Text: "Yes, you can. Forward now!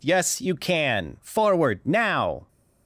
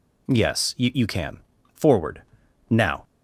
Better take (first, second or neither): first